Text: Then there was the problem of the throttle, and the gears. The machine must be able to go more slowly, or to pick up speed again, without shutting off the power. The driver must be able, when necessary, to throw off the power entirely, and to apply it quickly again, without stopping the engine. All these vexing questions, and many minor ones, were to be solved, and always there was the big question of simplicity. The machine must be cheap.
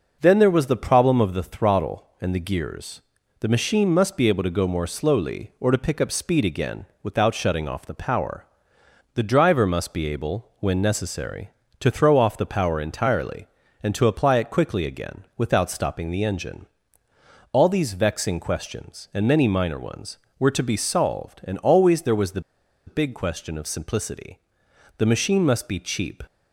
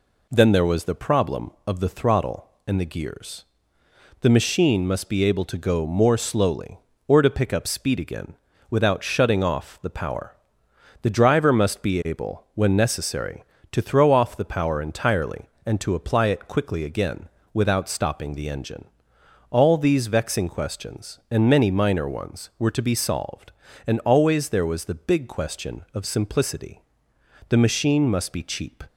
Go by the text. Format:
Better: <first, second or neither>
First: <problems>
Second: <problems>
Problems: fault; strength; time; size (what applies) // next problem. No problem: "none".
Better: second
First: pauses between "the" and "big"; noticeable; at 22.4 s; 0.46 s long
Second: none